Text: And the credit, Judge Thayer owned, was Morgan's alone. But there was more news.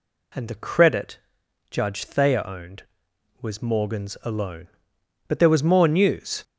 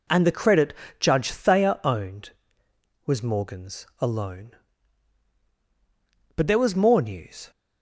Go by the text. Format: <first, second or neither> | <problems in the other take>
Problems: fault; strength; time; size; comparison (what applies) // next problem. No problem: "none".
neither | none